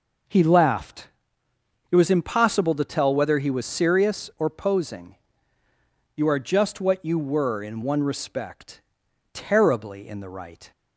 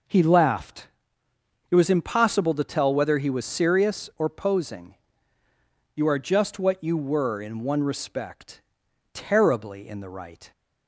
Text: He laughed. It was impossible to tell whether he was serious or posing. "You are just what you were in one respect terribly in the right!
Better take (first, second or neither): neither